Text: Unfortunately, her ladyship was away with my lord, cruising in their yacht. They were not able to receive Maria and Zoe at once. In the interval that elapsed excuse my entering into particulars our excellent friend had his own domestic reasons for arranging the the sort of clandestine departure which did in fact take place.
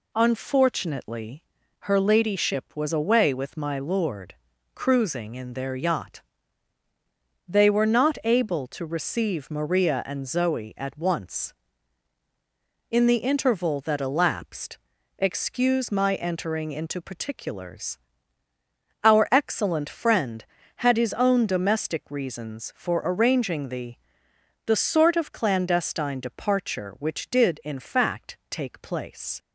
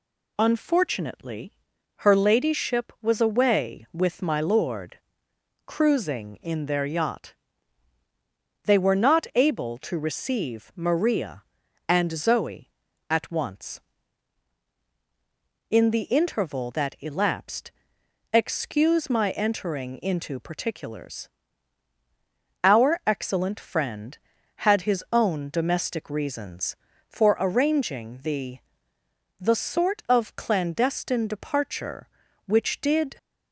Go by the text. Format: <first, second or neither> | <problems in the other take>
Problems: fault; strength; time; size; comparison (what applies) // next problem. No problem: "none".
first | pauses between "elapsed" and "excuse"; noticeable; at 17.7 s; 0.62 s long; also in the first // pauses between "particulars" and "our"; strong; at 21.2 s; 1.3 s long; also in the first // pauses between "the" and "the"; noticeable; at 28.5 s; 0.82 s long; noticeable in the first // stops before "in fact take place"; at 33.1 s